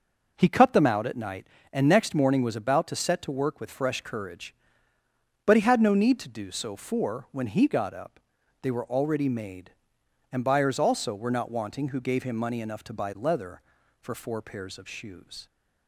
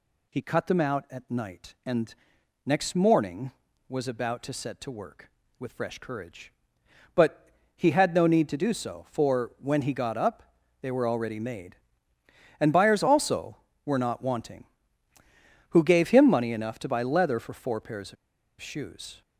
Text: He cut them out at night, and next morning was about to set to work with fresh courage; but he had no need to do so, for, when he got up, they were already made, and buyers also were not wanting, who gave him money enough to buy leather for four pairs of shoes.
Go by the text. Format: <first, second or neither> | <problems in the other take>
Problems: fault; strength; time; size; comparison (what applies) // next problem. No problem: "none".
first | pauses between "and" and "next"; noticeable; at 2.1 s; 0.54 s long // pauses between "but" and "he"; slight; at 7.4 s; 0.26 s long // pauses between "of" and "shoes"; at 18.1 s; 0.45 s long